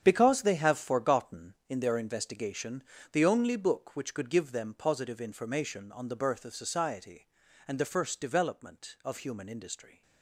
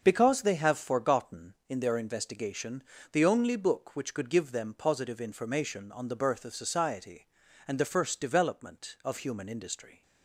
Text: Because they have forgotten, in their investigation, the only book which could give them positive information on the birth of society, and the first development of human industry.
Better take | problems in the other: second | gets quieter; strong; throughout; 11.5 dB // starts louder than the rest; strong; until 1.0 s; 8.5 dB; also in the second

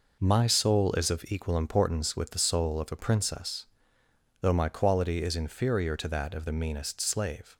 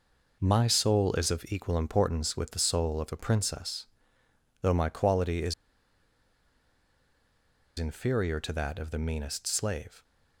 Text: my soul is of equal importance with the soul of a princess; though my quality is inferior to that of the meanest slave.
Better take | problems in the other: first | pauses between "is" and "inferior"; strong; at 5.5 s; 2.2 s long

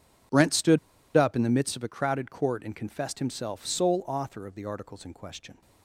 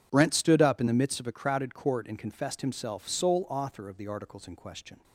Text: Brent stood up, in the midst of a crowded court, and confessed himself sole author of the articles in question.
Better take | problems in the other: second | pauses between "stood" and "up"; at 0.7 s; 0.38 s long

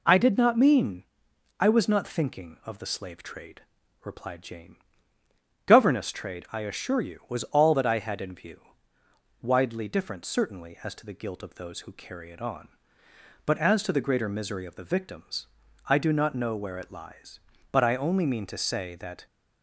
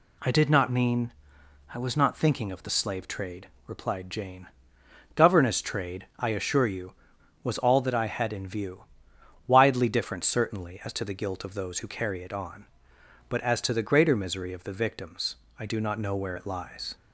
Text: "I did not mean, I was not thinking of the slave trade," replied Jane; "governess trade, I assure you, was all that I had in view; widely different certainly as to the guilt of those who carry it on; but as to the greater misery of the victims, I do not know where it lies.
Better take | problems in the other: second | goes on to say "But I only mean to say that"; from 17.7 s on; 1.5 s long

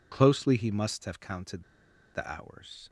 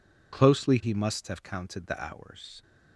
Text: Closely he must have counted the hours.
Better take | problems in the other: second | pauses between "counted" and "the"; noticeable; at 1.6 s; 0.51 s long

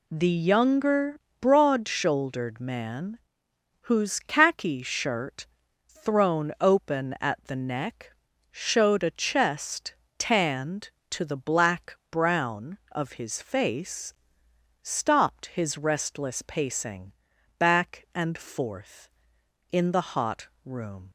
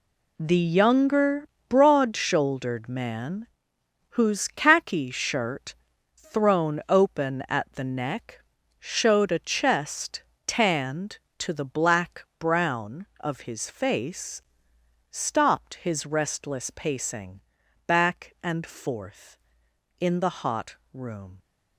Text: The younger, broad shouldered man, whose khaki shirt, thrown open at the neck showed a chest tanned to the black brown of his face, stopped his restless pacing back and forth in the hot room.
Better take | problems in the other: first | gets quieter; strong; throughout; 9.5 dB // pauses between "neck" and "showed"; at 8.3 s; 0.38 s long; also in the first // pauses between "chest" and "tanned"; slight; at 10.2 s; 0.22 s long; slight in the first // pauses between "pacing" and "back"; noticeable; at 17.3 s; 0.48 s long; noticeable in the first // pauses between "hot" and "room"; slight; at 20.7 s; 0.16 s long; slight in the first

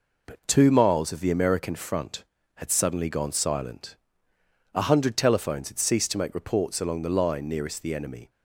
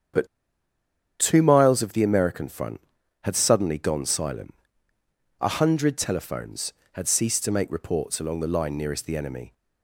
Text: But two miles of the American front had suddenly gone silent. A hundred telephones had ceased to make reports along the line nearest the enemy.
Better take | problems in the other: first | starts louder than the rest; strong; until 2.0 s; 8 dB // pauses between "But" and "two"; noticeable; at 0.2 s; 0.93 s long

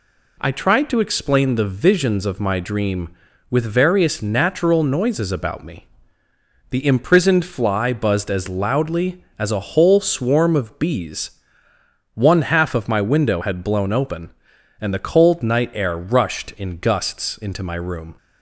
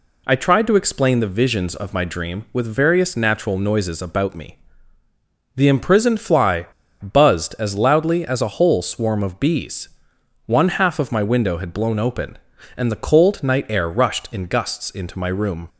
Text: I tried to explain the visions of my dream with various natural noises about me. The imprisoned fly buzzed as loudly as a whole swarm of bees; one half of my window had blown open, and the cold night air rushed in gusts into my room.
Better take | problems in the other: first | pauses between "fly" and "buzzed"; slight; at 6.6 s; 0.35 s long

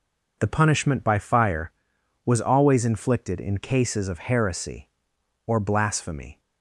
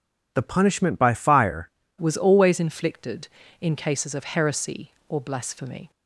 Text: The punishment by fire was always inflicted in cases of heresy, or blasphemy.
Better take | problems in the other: first | changes voice at "was"; from 1.9 s on; 4.0 s long

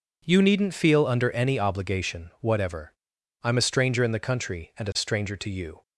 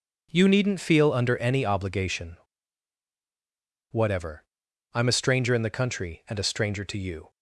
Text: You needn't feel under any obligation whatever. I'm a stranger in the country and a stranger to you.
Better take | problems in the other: first | pauses between "obligation" and "whatever"; strong; at 2.3 s; 1.5 s long

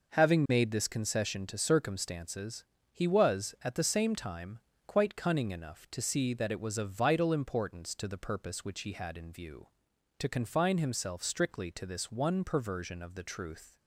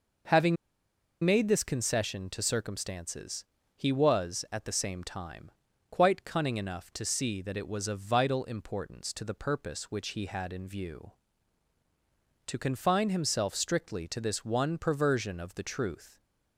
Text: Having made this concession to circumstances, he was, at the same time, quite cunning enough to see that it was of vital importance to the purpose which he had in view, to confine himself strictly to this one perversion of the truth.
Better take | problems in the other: first | pauses between "Having" and "made"; noticeable; at 0.5 s; 0.67 s long

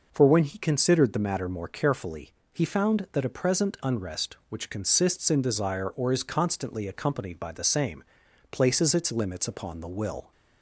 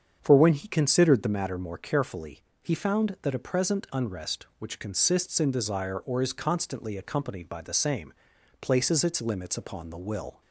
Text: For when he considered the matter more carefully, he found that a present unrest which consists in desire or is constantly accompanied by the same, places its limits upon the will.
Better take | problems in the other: first | starts louder than the rest; strong; until 1.4 s; 7.5 dB

